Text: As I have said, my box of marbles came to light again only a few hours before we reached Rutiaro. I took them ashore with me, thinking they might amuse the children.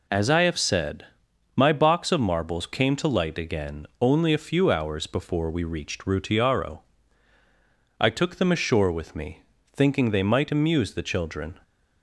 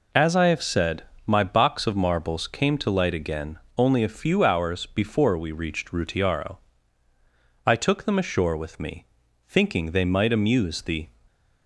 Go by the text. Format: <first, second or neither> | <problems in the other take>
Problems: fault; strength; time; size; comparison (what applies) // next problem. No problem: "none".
first | pauses between "again" and "only"; slight; at 3.5 s; 0.18 s long // stops before "children"; at 11.2 s